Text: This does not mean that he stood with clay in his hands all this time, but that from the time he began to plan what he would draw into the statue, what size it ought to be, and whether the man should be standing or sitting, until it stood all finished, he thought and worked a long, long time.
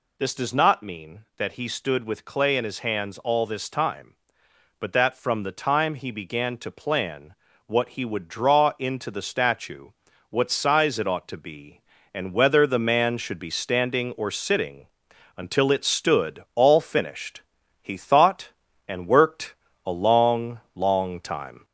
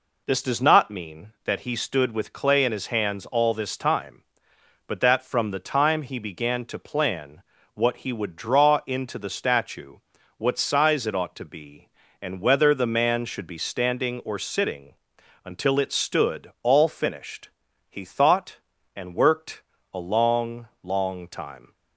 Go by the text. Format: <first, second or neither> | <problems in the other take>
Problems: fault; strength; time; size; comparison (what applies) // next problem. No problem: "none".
second | gets louder; slight; throughout; 3 dB // pauses between "plan" and "what"; slight; at 7.3 s; 0.32 s long; slight in the second // pauses between "worked" and "a"; slight; at 19.5 s; 0.30 s long; slight in the second